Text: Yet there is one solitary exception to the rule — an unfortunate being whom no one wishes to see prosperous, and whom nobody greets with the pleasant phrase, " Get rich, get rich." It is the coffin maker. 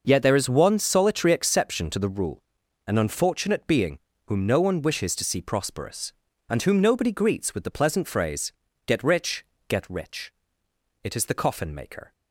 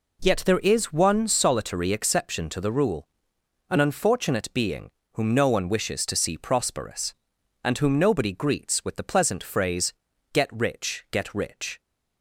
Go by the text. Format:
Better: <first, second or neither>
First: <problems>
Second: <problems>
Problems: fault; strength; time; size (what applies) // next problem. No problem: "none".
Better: first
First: pauses between "being" and "whom"; slight; at 3.9 s; 0.28 s long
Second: pauses between "being" and "whom"; slight; at 4.9 s; 0.24 s long // stops before "It is the coffin maker"; at 11.8 s